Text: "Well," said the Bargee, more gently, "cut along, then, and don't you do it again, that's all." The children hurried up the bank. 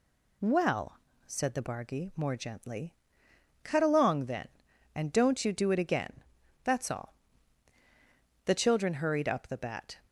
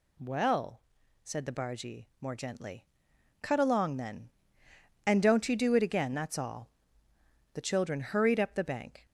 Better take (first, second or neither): second